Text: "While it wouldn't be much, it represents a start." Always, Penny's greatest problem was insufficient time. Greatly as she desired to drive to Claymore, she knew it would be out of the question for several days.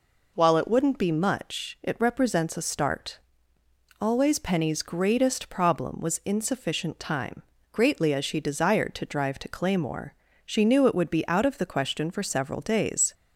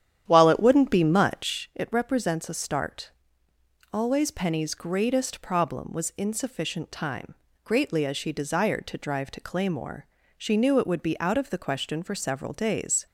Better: first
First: none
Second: starts louder than the rest; strong; until 1.7 s; 10 dB

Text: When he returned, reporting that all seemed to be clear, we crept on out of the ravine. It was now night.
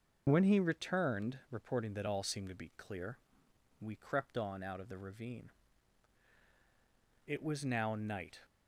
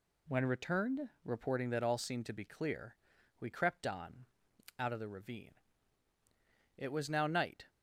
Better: first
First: none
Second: skips "he"; at 0.4 s // pauses between "on" and "out"; noticeable; at 4.2 s; 0.54 s long

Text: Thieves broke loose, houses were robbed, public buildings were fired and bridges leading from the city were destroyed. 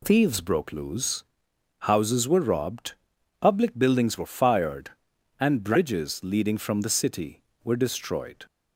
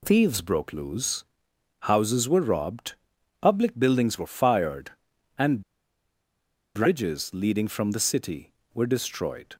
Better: first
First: none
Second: pauses between "and" and "bridges"; at 5.6 s; 1.1 s long

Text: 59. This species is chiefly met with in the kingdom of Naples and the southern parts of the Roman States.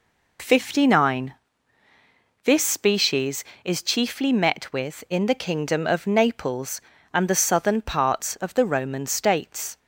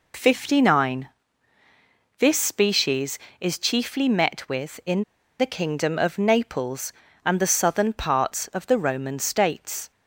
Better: first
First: none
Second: pauses between "in" and "the"; at 5.0 s; 0.36 s long

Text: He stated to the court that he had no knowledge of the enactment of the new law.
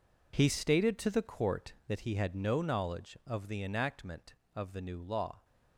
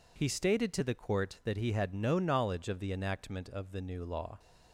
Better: second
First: gets quieter; strong; throughout; 13 dB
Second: none

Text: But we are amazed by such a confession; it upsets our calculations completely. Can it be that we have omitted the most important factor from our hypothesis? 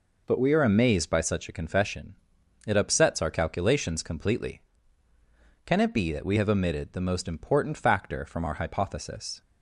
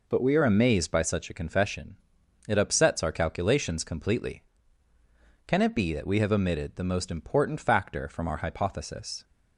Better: neither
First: none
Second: none

